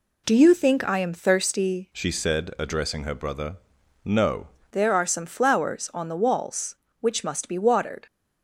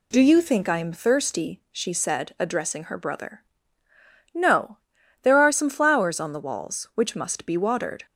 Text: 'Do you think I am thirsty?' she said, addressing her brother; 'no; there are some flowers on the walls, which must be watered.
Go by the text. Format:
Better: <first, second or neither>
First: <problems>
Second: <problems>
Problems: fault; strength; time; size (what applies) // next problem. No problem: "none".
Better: second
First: changes voice from "she" to "no"; from 1.9 to 4.4 s; 2.5 s long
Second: none